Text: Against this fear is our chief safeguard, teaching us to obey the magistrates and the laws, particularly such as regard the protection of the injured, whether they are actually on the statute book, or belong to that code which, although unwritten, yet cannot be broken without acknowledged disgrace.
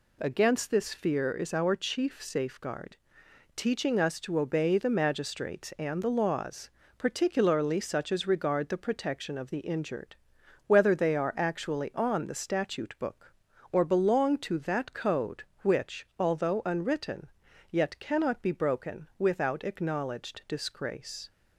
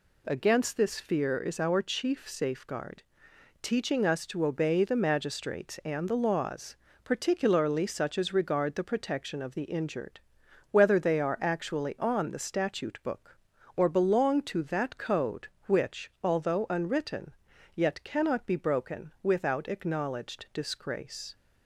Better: neither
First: none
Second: none

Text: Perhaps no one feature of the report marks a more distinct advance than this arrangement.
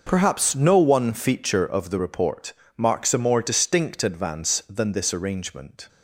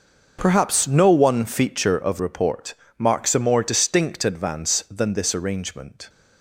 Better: first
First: pauses between "report" and "marks"; slight; at 2.5 s; 0.26 s long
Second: skips "the"; at 2.1 s // pauses between "report" and "marks"; slight; at 2.7 s; 0.26 s long

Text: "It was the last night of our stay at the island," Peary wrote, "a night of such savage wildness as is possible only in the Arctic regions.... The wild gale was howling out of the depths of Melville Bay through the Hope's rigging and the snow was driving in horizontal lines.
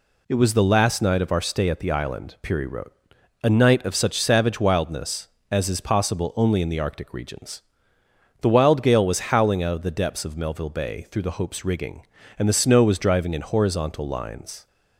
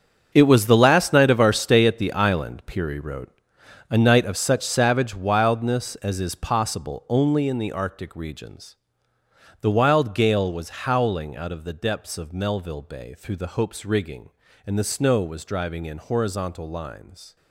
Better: first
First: none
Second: gets quieter; strong; throughout; 13.5 dB

